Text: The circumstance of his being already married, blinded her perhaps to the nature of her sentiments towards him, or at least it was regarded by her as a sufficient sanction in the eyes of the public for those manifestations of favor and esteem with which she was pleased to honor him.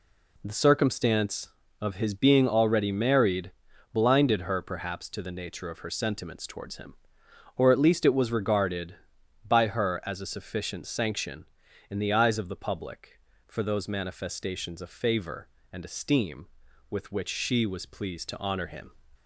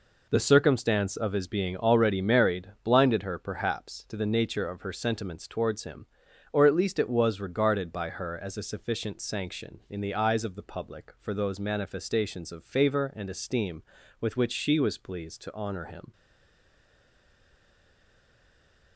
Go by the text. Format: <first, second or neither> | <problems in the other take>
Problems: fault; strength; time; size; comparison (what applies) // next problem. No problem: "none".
first | stays silent after the last word; strong; from 16.1 s on; 2.8 s long